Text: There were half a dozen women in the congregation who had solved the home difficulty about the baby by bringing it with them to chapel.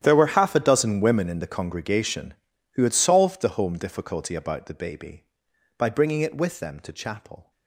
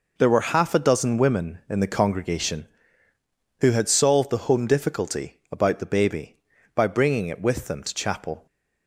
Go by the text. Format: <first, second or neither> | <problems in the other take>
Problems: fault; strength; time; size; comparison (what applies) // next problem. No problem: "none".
second | gets quieter; strong; throughout; 18 dB